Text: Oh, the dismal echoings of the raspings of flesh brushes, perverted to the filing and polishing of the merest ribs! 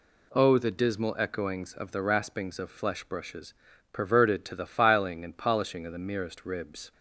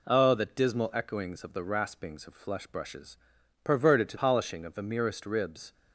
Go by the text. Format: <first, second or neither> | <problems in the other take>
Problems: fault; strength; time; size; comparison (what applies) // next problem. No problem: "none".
first | skips "the filing and"; at 4.1 s